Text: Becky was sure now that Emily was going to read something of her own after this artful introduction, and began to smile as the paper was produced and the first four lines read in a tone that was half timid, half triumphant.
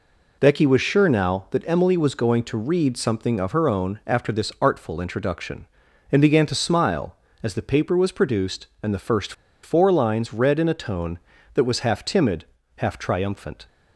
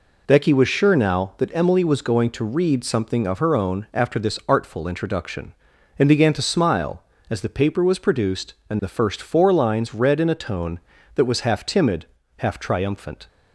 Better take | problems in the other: second | pauses between "first" and "four"; slight; at 9.3 s; 0.31 s long

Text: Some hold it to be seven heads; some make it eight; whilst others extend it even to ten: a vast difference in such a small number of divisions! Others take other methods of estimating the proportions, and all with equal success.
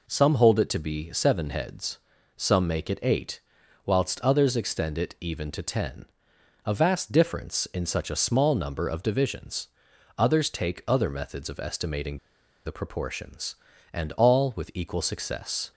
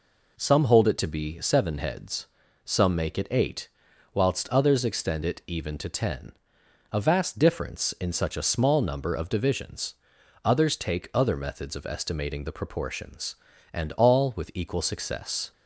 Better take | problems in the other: second | pauses between "estimating" and "the"; noticeable; at 12.1 s; 0.46 s long

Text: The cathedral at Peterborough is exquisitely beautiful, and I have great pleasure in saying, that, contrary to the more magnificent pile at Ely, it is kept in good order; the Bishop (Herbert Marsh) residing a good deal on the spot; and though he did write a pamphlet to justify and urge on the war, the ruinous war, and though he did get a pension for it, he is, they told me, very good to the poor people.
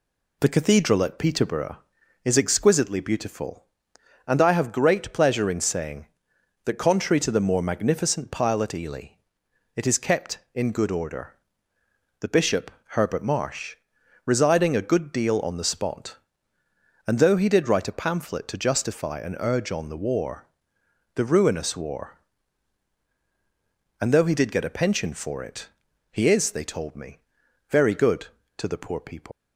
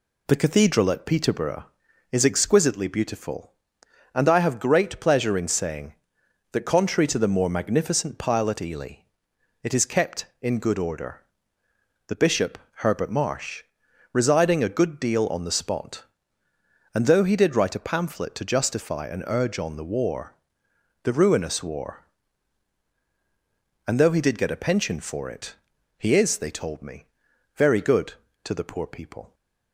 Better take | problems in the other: second | leaves "people" unfinished; at 29.3 s; 155 ms

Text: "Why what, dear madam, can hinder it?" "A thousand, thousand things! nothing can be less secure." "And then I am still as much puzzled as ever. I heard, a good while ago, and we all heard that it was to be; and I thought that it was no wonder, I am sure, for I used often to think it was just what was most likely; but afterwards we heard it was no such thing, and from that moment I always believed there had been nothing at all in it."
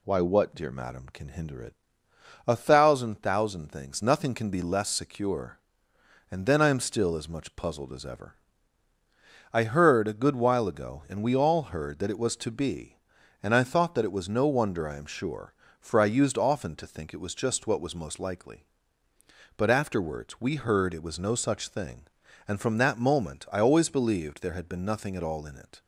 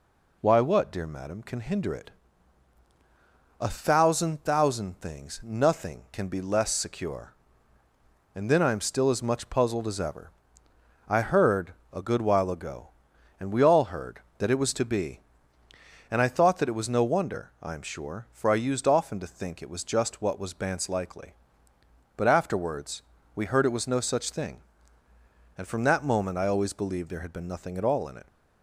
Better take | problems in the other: first | says "bance" for "most"; at 20.5 s // pauses between "afterwards" and "we"; slight; at 23.0 s; 0.32 s long

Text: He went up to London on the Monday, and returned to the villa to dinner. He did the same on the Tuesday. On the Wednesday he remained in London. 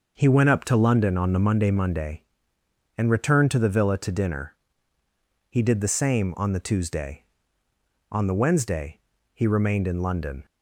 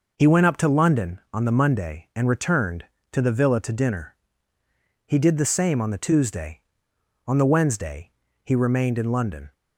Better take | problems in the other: second | starts louder than the rest; noticeable; until 1.2 s; 6 dB // says "Monday" twice; at 1.7 s // pauses between "Wednesday" and "he"; slight; at 8.9 s; 0.34 s long; slight in the second

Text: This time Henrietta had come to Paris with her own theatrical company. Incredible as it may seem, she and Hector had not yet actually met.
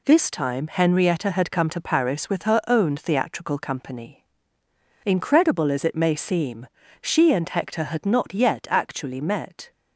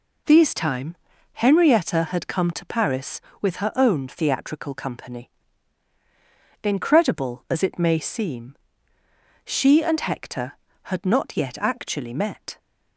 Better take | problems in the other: first | says "These" for "This"; at 0.2 s // pauses between "time" and "Henrietta"; at 0.9 s; 0.38 s long

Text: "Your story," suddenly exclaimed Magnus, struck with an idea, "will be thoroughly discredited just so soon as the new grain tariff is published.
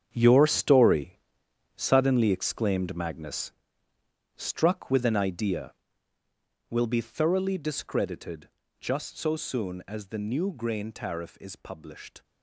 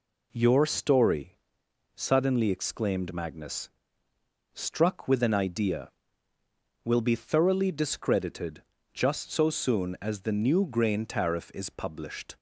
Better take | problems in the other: second | gets quieter; strong; throughout; 11.5 dB // pauses between "discredited" and "just"; slight; at 8.4 s; 0.32 s long; slight in the second

